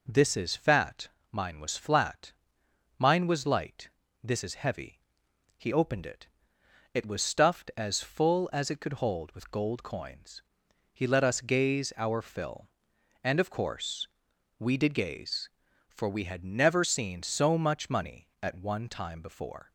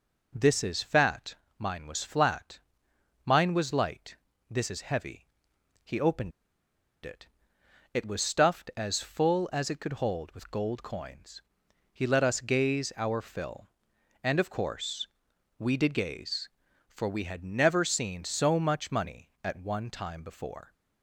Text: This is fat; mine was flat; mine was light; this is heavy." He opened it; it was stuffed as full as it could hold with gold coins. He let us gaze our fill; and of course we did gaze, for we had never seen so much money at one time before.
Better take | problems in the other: first | pauses between "opened" and "it"; noticeable; at 6.3 s; 0.74 s long // pauses between "course" and "we"; noticeable; at 15.0 s; 0.54 s long; noticeable in the first

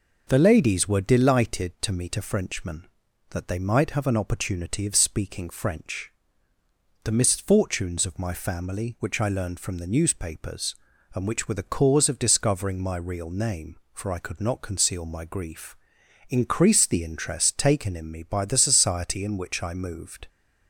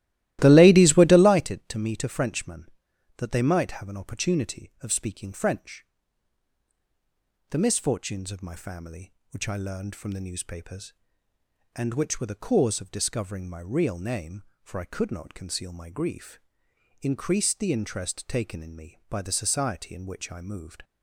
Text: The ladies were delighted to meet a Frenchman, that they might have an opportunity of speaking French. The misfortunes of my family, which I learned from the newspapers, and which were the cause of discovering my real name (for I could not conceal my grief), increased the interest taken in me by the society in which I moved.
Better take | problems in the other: first | starts louder than the rest; strong; until 1.4 s; 15.5 dB

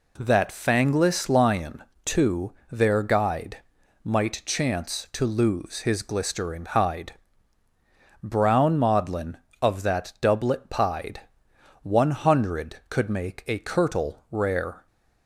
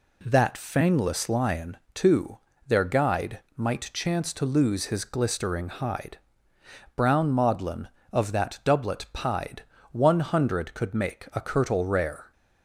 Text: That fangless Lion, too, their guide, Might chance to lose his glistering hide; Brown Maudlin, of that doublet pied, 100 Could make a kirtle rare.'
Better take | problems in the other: neither | none

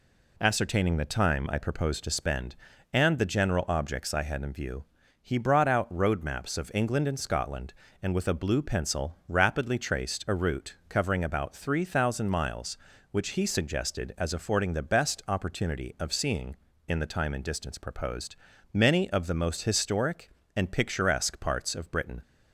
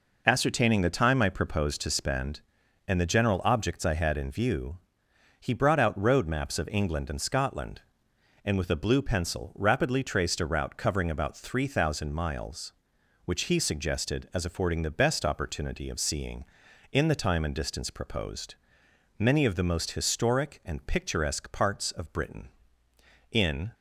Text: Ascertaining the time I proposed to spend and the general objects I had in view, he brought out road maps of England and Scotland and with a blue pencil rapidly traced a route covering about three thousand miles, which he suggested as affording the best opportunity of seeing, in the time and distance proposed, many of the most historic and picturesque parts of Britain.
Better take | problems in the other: first | goes on to say "In"; slight; from 23.3 s on; 0.40 s long

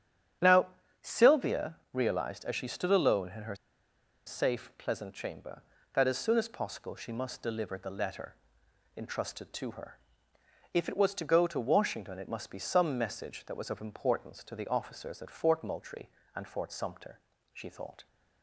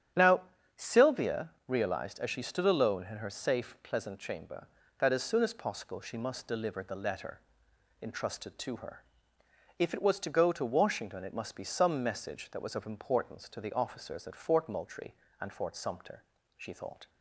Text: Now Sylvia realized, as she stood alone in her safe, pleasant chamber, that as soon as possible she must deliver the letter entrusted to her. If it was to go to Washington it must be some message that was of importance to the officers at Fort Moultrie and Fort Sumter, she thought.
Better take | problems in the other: second | starts louder than the rest; strong; until 1.7 s; 9 dB; strong in the second // pauses between "Now" and "Sylvia"; slight; at 0.6 s; 0.34 s long; slight in the second // pauses between "Sylvia" and "realized"; slight; at 1.7 s; 0.16 s long; slight in the second // pauses between "her" and "safe"; noticeable; at 3.5 s; 0.71 s long // pauses between "letter" and "entrusted"; noticeable; at 8.3 s; 0.62 s long; noticeable in the second

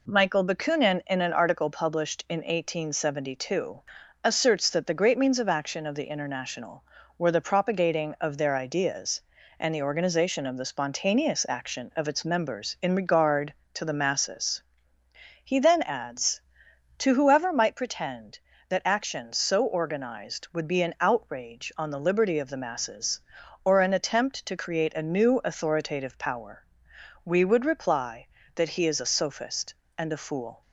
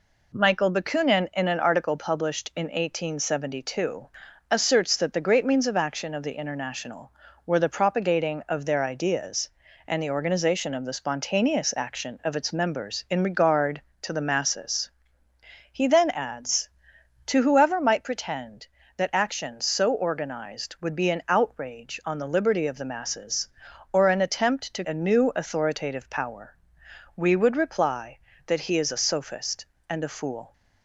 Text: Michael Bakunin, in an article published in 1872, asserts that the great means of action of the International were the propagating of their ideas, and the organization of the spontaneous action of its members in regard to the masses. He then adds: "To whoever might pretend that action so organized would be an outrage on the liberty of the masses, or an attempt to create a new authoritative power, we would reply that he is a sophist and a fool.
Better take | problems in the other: first | skips "create"; at 24.8 s

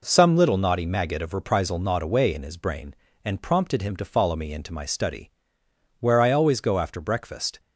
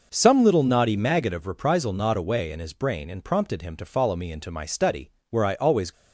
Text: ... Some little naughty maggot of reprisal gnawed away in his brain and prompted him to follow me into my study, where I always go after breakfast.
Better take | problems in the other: first | stops before "go after breakfast"; at 5.9 s

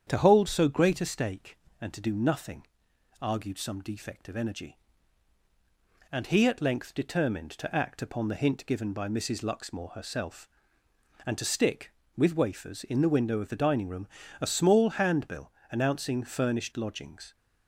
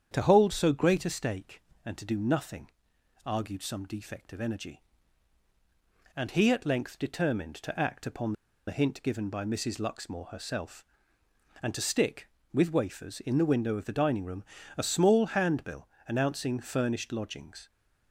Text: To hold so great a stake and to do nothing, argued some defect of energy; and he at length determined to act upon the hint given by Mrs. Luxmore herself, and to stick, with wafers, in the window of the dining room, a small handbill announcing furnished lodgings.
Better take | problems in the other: first | starts louder than the rest; strong; until 1.1 s; 8.5 dB; strong in the first // pauses between "upon" and "the"; slight; at 8.3 s; 0.35 s long // pauses between "handbill" and "announcing"; slight; at 15.8 s; 0.18 s long; slight in the first

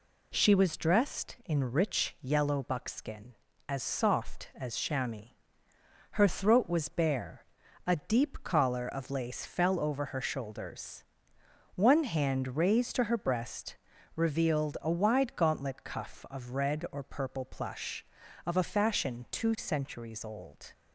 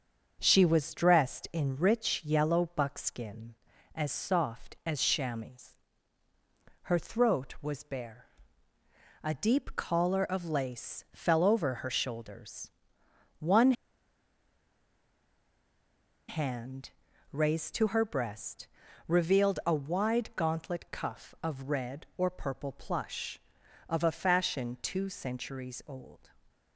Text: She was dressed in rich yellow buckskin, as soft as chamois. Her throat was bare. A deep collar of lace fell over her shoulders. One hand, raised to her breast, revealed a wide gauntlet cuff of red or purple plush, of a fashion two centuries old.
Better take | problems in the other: first | starts louder than the rest; until 1.4 s; 7 dB // pauses between "One" and "hand"; strong; at 13.7 s; 2.5 s long

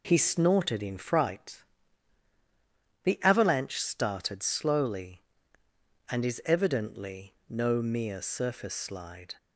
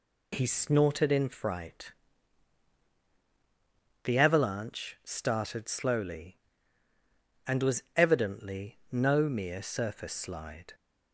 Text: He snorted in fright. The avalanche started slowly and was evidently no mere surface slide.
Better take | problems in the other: second | says "is" for "was"; at 6.2 s // pauses between "evidently" and "no"; slight; at 7.3 s; 0.16 s long

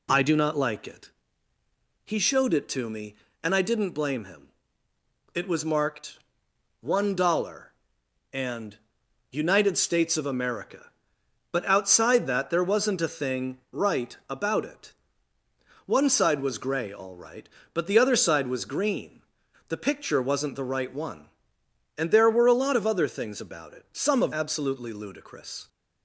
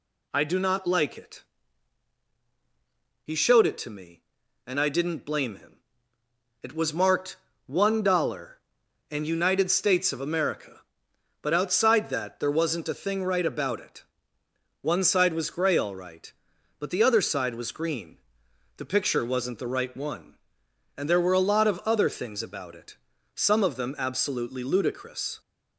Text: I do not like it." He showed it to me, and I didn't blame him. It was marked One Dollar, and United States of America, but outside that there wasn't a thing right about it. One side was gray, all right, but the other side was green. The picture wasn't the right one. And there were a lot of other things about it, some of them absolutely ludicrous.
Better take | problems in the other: second | pauses between "marked" and "One"; noticeable; at 6.1 s; 0.64 s long; slight in the second // pauses between "and" and "United"; noticeable; at 8.7 s; 0.52 s long // skips "them"; at 24.3 s

